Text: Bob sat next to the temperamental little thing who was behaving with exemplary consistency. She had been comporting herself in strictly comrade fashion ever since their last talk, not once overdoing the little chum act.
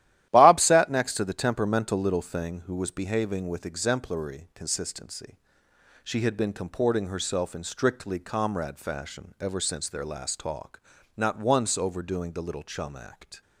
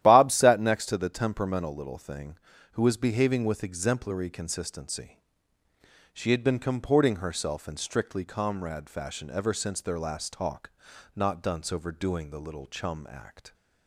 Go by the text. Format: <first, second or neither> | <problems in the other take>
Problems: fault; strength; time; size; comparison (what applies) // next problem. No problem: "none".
first | starts louder than the rest; strong; until 1.0 s; 12.5 dB; strong in the first // says "dunce" for "once"; at 11.4 s